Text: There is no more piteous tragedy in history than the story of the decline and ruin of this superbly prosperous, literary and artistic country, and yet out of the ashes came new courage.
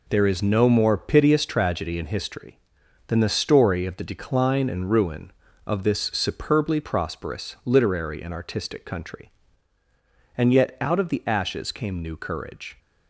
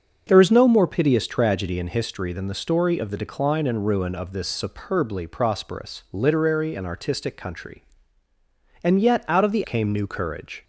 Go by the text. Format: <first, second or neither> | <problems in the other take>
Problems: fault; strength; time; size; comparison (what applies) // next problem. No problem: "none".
first | starts louder than the rest; until 1.2 s; 6.5 dB // skips "ashes"; at 9.6 s